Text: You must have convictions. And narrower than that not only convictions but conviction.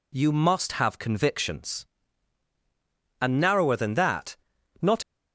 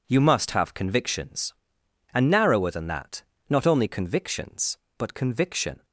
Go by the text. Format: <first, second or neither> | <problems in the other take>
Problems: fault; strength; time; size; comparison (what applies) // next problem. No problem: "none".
second | pauses between "that" and "not"; at 4.3 s; 0.44 s long; slight in the second // stops before "only convictions but conviction"; at 5.0 s